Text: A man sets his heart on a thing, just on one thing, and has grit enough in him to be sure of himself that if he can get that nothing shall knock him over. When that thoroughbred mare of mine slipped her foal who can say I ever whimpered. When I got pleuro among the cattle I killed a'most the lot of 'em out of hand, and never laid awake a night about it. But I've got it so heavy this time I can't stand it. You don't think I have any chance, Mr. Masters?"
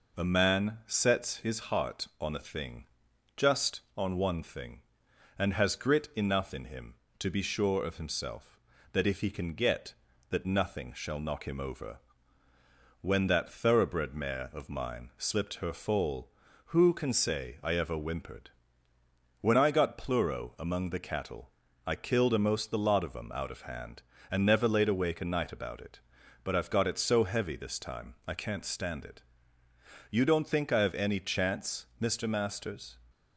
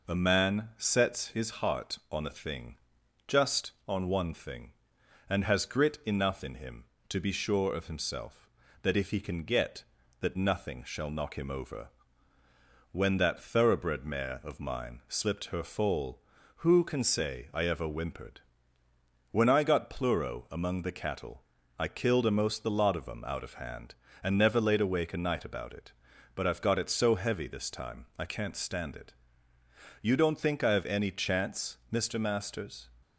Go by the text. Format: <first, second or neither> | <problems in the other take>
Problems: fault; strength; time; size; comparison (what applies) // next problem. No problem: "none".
neither | pauses between "cattle" and "I"; slight; the same in both